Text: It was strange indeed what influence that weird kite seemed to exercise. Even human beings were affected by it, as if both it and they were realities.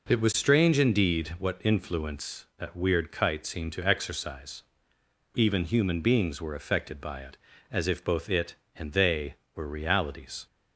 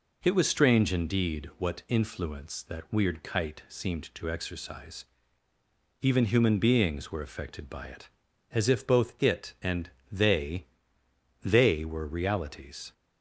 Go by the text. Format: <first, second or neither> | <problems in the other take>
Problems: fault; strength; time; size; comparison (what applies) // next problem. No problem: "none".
first | pauses between "and" and "they"; slight; at 9.9 s; 0.20 s long // says "they" twice; at 11.4 s